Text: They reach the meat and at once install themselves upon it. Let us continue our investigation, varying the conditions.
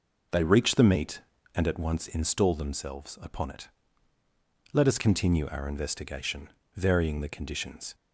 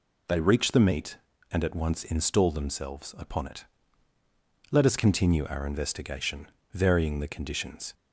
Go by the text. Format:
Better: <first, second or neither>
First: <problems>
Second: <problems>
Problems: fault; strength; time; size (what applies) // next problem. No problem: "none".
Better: second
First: starts louder than the rest; noticeable; until 1.9 s; 5 dB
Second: none